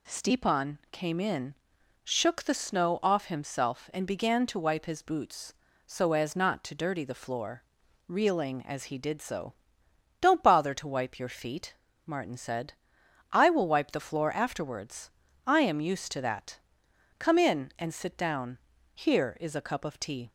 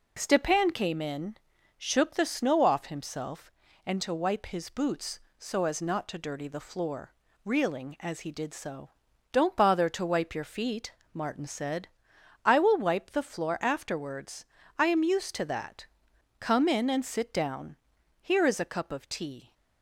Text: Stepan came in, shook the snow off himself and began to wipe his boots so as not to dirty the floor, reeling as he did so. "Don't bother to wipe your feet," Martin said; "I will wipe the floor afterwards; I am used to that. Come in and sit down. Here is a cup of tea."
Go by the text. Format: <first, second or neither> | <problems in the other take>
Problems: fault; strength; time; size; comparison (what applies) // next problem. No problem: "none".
first | skips "began"; at 3.9 s